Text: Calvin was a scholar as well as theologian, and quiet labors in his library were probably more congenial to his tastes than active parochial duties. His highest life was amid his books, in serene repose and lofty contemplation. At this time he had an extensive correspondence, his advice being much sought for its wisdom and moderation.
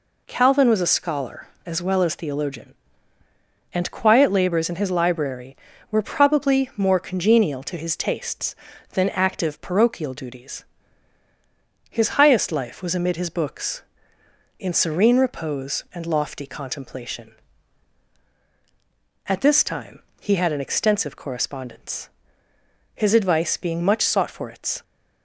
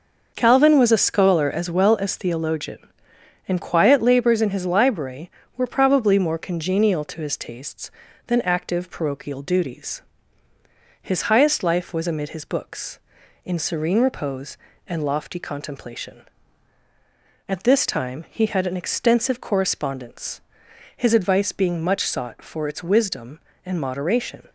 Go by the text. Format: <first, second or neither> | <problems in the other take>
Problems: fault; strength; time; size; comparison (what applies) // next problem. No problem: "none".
second | pauses between "time" and "he"; slight; at 20.0 s; 0.18 s long // stops before "wisdom and moderation"; at 24.8 s